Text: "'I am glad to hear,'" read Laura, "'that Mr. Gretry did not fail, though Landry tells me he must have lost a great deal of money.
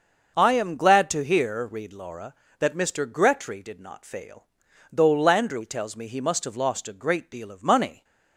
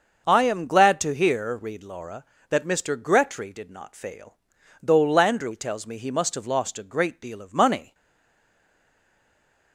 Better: first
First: starts louder than the rest; until 1.3 s; 6.5 dB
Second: starts louder than the rest; until 1.2 s; 6.5 dB // stays silent after the last word; noticeable; from 7.9 s on; 1.8 s long

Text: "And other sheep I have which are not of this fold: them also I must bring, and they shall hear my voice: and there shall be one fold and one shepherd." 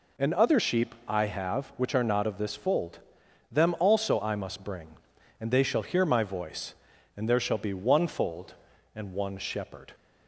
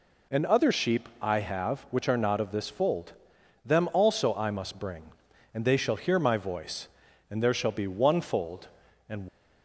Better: first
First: none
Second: stops before "one shepherd"; at 9.2 s

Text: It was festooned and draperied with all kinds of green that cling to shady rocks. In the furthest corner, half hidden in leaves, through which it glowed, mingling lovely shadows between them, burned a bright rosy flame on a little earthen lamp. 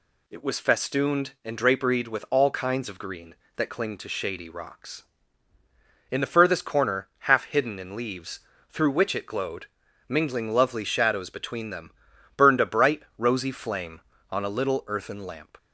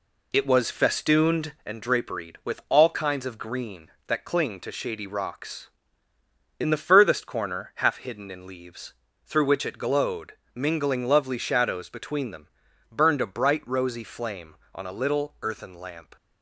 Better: first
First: none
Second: starts louder than the rest; slight; until 1.7 s; 2.5 dB

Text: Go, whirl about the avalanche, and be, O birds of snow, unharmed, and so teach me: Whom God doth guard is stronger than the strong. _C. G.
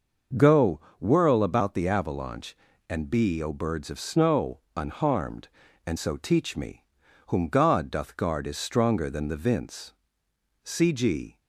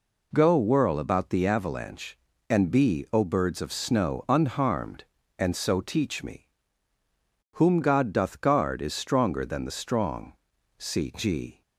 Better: second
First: starts louder than the rest; noticeable; until 1.5 s; 6 dB // says "vince" for "strong"; at 9.3 s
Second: none

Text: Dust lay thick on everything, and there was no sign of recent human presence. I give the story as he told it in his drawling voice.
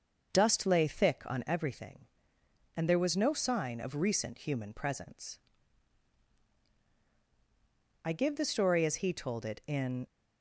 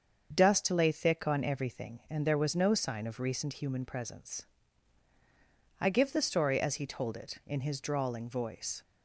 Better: second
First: starts louder than the rest; until 1.3 s; 6.5 dB // stops before "his drawling voice"; at 10.0 s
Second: starts louder than the rest; until 1.3 s; 7 dB

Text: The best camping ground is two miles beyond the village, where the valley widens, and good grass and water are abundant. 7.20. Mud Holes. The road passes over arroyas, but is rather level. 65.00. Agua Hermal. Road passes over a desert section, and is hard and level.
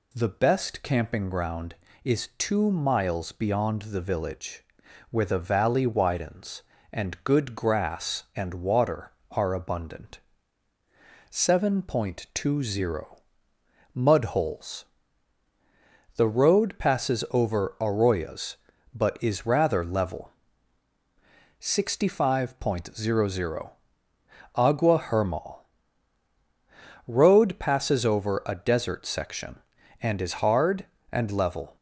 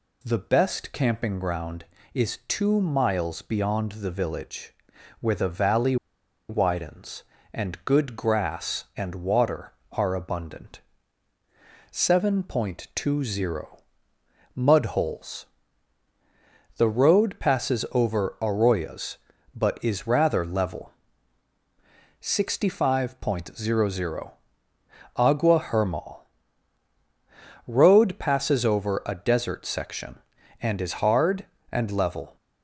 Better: first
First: none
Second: pauses between "valley" and "widens"; noticeable; at 5.9 s; 0.54 s long

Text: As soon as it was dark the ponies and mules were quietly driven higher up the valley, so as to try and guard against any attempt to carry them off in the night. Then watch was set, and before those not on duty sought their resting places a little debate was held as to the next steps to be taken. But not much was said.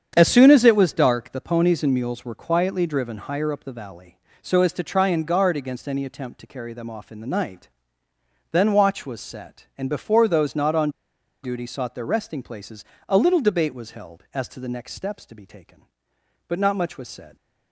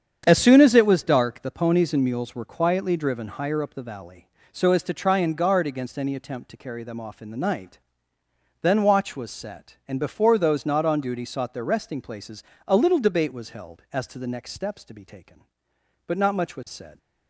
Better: second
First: starts louder than the rest; strong; until 1.1 s; 8 dB // pauses between "on" and "duty"; noticeable; at 10.9 s; 0.53 s long // pauses between "places" and "a"; slight; at 12.8 s; 0.24 s long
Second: starts louder than the rest; strong; until 1.2 s; 8 dB // pauses between "places" and "a"; slight; at 12.4 s; 0.24 s long

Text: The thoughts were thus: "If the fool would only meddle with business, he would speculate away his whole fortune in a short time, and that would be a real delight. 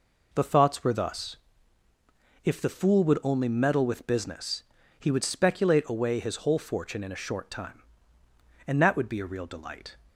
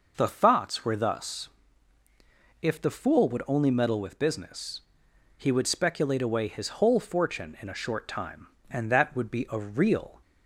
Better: first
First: none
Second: stops before "delight"; at 10.2 s

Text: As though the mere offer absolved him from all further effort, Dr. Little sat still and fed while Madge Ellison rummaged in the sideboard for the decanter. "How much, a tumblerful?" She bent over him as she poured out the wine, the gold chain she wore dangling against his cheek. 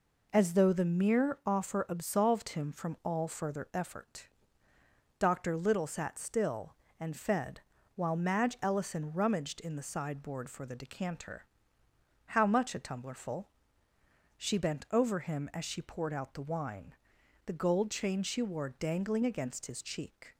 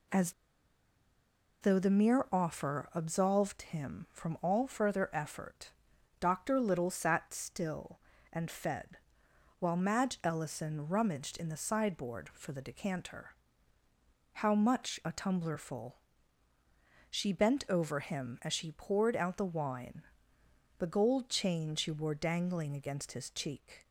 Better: first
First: pauses between "fed" and "while"; slight; at 7.6 s; 0.34 s long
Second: pauses between "As" and "though"; strong; at 0.3 s; 1.2 s long // pauses between "fed" and "while"; noticeable; at 8.9 s; 0.60 s long

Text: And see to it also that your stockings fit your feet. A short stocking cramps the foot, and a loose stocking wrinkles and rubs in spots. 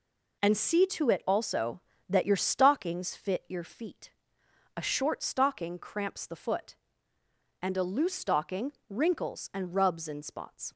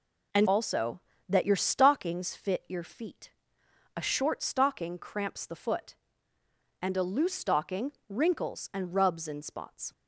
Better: first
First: pauses between "stocking" and "wrinkles"; slight; at 8.7 s; 0.16 s long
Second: skips "see to it"; at 0.4 s // pauses between "stocking" and "wrinkles"; slight; at 7.9 s; 0.16 s long

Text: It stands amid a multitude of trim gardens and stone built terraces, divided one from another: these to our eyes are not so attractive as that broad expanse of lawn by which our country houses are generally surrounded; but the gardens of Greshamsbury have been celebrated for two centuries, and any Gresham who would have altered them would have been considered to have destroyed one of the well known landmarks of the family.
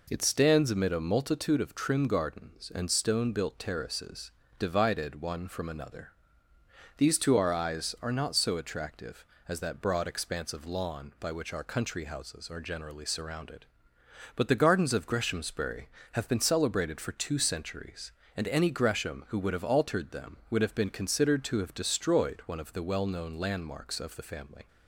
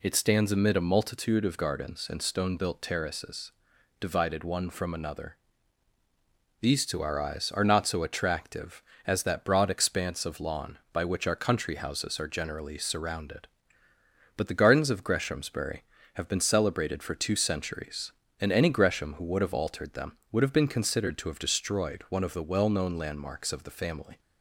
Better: first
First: none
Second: skips "trim"; at 1.5 s

